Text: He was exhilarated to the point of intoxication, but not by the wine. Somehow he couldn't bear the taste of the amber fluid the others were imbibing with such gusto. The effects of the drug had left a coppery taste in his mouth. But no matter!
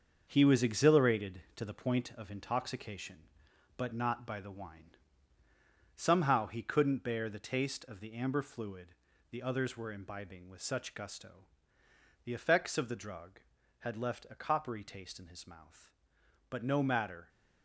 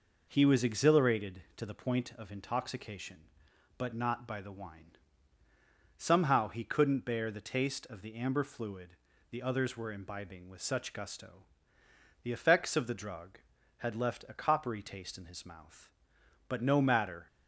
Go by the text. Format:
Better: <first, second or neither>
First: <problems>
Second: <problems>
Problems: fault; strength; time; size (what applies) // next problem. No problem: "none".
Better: second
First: gets quieter; throughout; 7 dB // pauses between "fluid" and "the"; at 8.8 s; 0.42 s long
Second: pauses between "fluid" and "the"; at 8.8 s; 0.40 s long